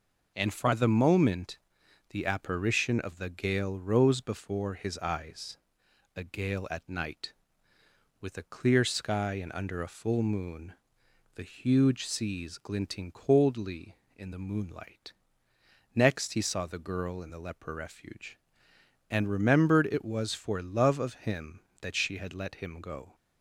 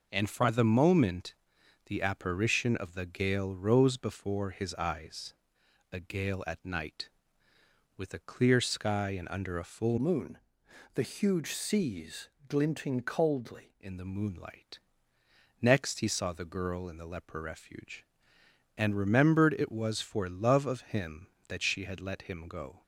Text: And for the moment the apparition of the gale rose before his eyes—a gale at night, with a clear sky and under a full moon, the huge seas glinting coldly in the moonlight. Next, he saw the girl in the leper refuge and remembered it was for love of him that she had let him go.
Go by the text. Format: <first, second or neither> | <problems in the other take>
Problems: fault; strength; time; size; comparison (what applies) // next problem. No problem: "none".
first | pauses between "moment" and "the"; noticeable; at 1.3 s; 0.52 s long; noticeable in the first // changes voice from "moon" to "coldly"; from 9.9 to 13.7 s; 3.8 s long // pauses between "seas" and "glinting"; slight; at 12.2 s; 0.18 s long